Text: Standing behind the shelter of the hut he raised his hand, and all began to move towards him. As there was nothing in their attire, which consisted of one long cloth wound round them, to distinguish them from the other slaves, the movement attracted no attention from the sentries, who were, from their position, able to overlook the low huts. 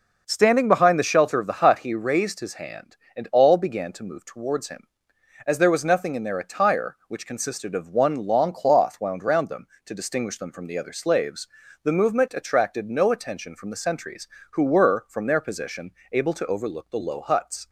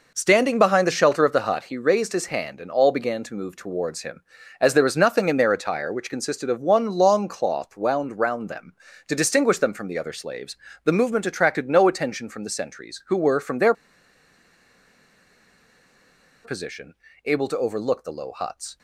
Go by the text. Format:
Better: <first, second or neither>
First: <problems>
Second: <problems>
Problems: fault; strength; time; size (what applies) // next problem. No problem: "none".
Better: first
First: none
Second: pauses between "their" and "position"; strong; at 13.7 s; 2.7 s long